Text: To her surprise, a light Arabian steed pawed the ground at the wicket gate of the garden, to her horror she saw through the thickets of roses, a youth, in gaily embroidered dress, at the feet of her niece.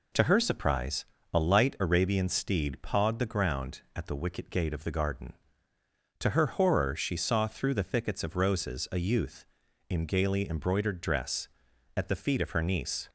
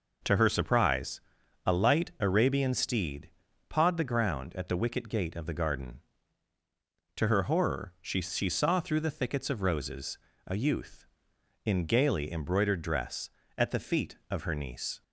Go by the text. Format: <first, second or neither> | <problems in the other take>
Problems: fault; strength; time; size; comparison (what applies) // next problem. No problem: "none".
first | pauses between "steed" and "pawed"; at 3.2 s; 0.40 s long // says "she" twice; at 8.2 s